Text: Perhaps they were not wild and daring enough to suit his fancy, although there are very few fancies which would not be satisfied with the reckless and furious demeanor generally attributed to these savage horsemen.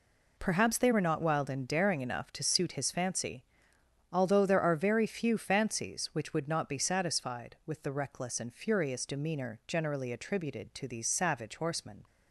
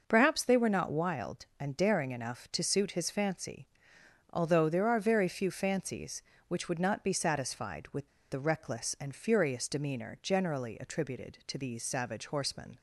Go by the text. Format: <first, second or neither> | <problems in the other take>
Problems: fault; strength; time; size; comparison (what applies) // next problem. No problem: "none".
first | pauses between "with" and "the"; slight; at 8.0 s; 0.22 s long